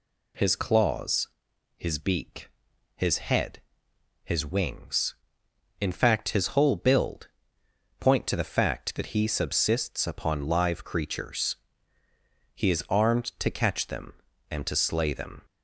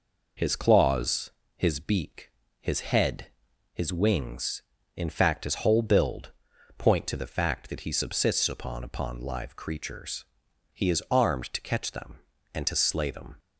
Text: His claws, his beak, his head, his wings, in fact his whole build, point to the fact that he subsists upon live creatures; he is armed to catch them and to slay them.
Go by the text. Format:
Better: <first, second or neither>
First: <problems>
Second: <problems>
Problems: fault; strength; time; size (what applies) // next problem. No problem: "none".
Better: first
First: none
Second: says "upon" twice; at 8.8 s